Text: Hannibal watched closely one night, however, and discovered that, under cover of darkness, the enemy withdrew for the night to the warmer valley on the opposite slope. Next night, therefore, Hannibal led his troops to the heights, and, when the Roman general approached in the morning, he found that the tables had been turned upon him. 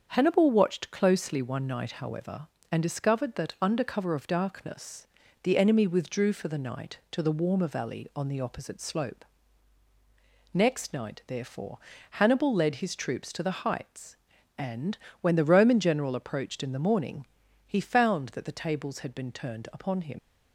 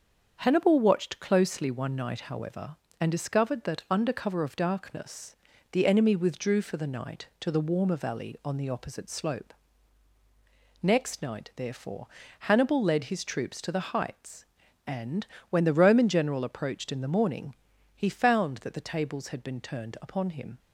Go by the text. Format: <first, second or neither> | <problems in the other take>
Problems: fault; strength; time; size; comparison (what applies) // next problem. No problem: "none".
second | starts louder than the rest; until 1.1 s; 7 dB; also in the second // leaves "him" unfinished; at 20.1 s; 105 ms